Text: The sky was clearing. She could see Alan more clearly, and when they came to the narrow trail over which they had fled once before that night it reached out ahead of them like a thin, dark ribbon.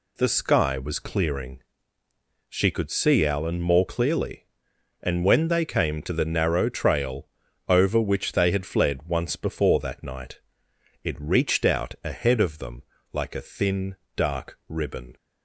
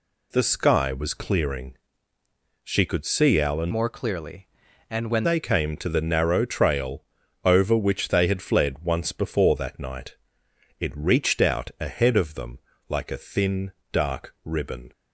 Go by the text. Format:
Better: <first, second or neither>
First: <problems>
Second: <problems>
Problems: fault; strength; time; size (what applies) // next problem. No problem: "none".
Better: first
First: pauses between "trail" and "over"; at 7.2 s; 0.42 s long // pauses between "night" and "it"; noticeable; at 10.3 s; 0.66 s long // pauses between "them" and "like"; slight; at 12.8 s; 0.30 s long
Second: changes voice from "more" to "when"; from 3.7 to 5.2 s; 1.5 s long // pauses between "trail" and "over"; at 7.0 s; 0.42 s long // pauses between "night" and "it"; noticeable; at 10.1 s; 0.66 s long // pauses between "them" and "like"; slight; at 12.5 s; 0.30 s long